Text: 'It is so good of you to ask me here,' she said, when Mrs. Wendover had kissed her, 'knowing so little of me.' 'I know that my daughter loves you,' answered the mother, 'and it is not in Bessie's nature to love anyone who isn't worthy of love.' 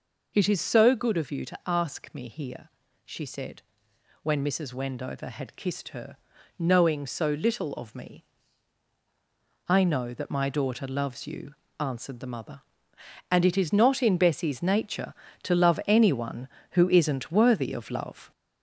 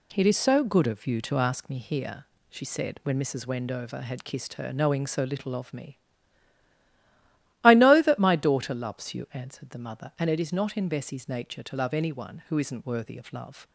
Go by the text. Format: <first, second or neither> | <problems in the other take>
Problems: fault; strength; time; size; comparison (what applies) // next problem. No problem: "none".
second | gets louder; noticeable; throughout; 4 dB